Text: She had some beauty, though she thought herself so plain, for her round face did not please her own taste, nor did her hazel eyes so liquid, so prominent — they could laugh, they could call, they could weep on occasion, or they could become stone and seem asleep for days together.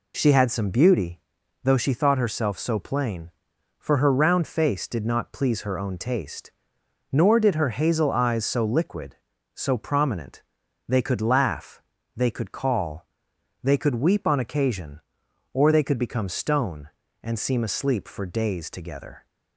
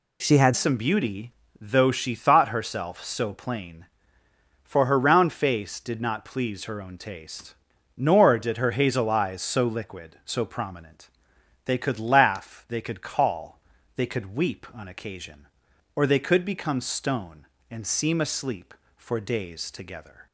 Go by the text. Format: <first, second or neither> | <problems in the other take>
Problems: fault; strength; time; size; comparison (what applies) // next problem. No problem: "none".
first | changes voice at "some"; from 0.5 s on; 19.7 s long